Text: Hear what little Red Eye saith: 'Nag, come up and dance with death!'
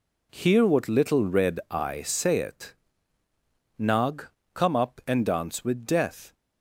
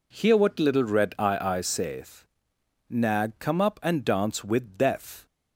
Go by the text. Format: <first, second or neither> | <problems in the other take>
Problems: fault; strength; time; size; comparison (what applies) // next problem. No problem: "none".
first | says "Eye" twice; at 1.3 s